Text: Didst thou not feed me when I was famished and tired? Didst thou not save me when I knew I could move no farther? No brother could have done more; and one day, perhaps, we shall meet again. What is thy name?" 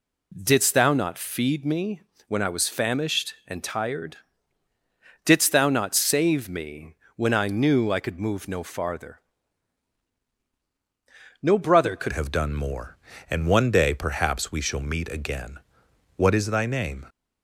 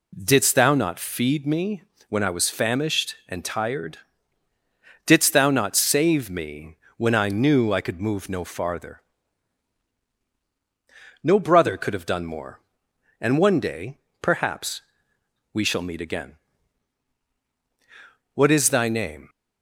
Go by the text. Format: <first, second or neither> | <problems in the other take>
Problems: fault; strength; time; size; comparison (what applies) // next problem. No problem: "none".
second | pauses between "me" and "when"; slight; at 2.0 s; 0.26 s long; slight in the second // pauses between "me" and "when"; slight; at 6.9 s; 0.22 s long; slight in the second // changes voice at "have"; from 12.1 s on; 4.9 s long